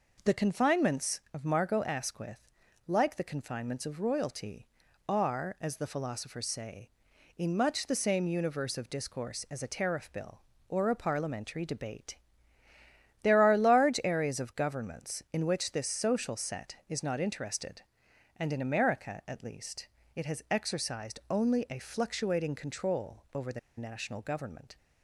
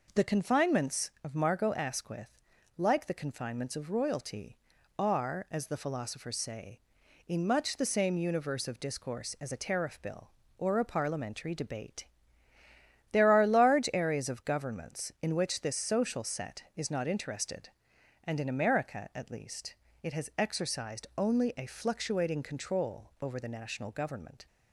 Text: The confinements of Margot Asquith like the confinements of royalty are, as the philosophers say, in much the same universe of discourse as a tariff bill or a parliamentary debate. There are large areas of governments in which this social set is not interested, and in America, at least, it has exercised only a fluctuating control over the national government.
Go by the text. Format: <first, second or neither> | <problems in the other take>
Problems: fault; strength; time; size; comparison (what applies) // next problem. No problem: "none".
second | pauses between "Asquith" and "like"; at 2.4 s; 0.40 s long; also in the second // pauses between "the" and "national"; slight; at 23.5 s; 0.18 s long